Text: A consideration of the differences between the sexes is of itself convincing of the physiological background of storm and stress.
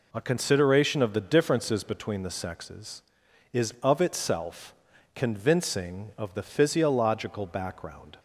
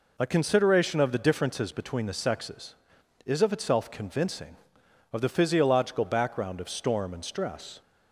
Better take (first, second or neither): second